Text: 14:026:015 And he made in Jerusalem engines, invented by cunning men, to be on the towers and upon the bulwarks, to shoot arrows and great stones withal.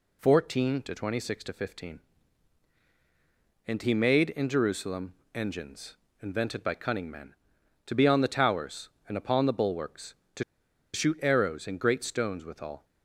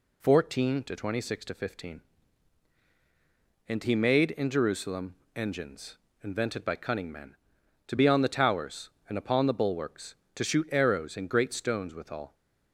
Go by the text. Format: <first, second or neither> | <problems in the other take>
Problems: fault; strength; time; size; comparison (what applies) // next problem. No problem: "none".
second | pauses between "Jerusalem" and "engines"; slight; at 5.1 s; 0.20 s long; slight in the second // pauses between "to" and "shoot"; noticeable; at 10.4 s; 0.50 s long